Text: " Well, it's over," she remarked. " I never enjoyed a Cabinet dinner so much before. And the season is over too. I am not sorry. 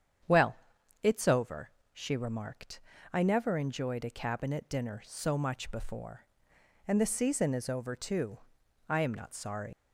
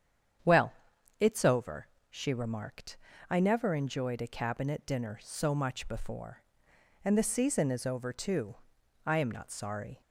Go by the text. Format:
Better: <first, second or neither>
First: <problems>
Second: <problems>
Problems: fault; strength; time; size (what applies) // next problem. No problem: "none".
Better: second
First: starts louder than the rest; strong; until 1.7 s; 8 dB // leaves "sorry" unfinished; at 9.7 s; 100 ms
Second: starts louder than the rest; strong; until 1.8 s; 8.5 dB